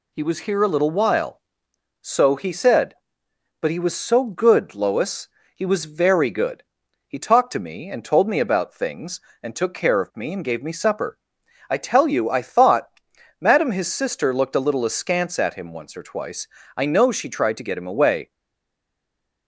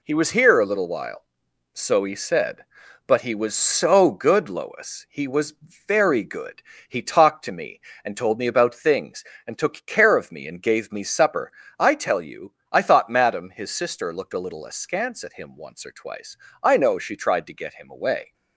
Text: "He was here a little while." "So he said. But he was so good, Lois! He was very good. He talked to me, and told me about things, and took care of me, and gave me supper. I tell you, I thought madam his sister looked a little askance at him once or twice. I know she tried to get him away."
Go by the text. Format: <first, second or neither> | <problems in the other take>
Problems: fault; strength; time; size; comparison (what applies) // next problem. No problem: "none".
second | pauses between "thought" and "madam"; noticeable; at 12.8 s; 0.50 s long // stays silent after the last word; noticeable; from 18.3 s on; 1.1 s long